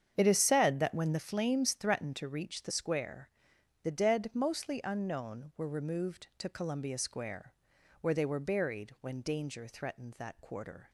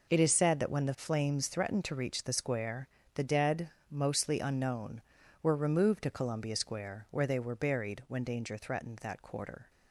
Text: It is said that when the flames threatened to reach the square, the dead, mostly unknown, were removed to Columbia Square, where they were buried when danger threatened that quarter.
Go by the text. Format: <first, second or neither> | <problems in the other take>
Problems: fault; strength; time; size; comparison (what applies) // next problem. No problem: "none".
second | starts louder than the rest; strong; until 1.3 s; 8 dB